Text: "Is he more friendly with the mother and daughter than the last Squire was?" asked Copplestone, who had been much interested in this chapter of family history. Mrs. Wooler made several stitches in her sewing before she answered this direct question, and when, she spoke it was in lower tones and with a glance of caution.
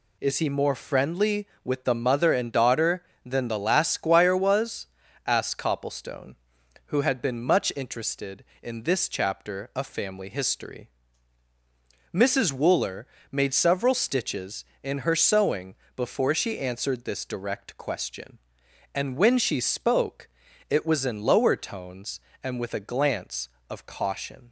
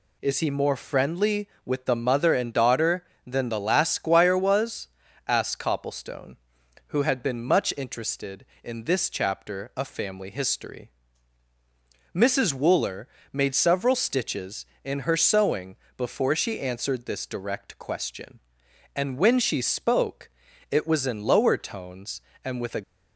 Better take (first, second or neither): first